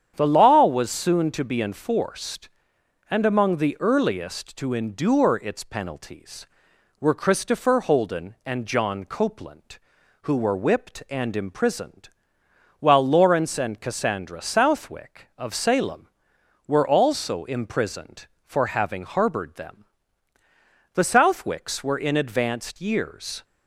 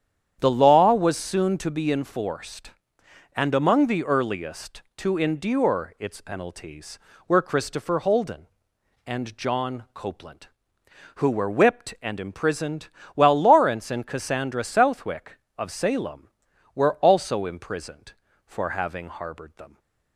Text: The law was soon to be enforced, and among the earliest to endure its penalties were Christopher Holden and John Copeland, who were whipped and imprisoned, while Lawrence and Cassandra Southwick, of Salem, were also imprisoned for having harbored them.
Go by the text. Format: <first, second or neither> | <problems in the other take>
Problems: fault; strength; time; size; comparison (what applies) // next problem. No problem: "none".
second | starts louder than the rest; strong; until 1.1 s; 8.5 dB; strong in the second // goes on to say "The Southwicks were in advanced years"; strong; from 20.9 s on; 2.5 s long